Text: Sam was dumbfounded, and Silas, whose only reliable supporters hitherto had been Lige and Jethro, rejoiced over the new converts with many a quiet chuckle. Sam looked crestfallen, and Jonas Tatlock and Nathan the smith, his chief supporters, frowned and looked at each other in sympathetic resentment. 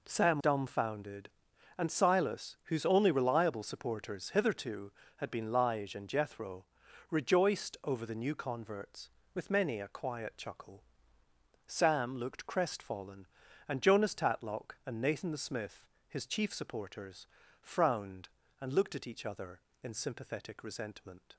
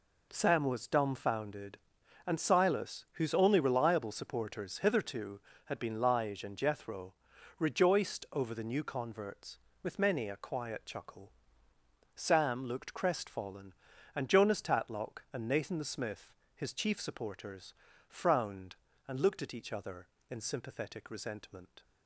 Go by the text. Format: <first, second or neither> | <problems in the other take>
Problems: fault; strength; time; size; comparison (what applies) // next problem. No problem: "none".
second | skips "was"; at 0.4 s